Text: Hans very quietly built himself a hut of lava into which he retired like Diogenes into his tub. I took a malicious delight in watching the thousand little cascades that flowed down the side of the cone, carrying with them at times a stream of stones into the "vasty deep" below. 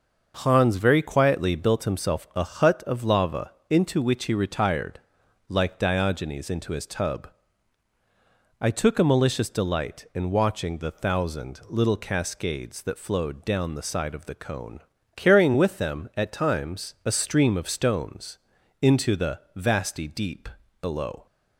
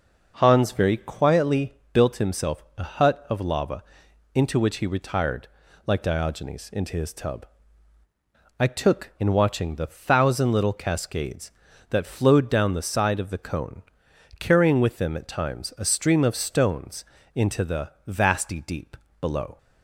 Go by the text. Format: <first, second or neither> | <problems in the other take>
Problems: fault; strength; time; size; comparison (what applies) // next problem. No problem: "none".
first | pauses between "quietly" and "built"; slight; at 1.7 s; 0.18 s long // pauses between "himself" and "a"; slight; at 2.6 s; 0.16 s long // pauses between "lava" and "into"; noticeable; at 3.8 s; 0.52 s long; slight in the first // pauses between "retired" and "like"; at 5.4 s; 0.40 s long; noticeable in the first // skips "a malicious delight"; at 9.1 s // pauses between "stones" and "into"; slight; at 17.0 s; 0.32 s long; also in the first // pauses between "the" and "vasty"; slight; at 17.8 s; 0.18 s long // pauses between "deep" and "below"; slight; at 18.9 s; 0.24 s long; slight in the first